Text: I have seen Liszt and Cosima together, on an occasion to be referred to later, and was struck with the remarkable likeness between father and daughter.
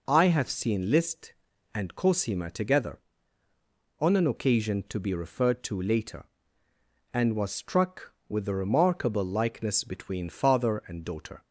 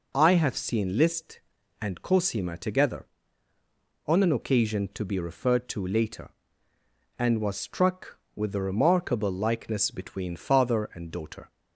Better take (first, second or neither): neither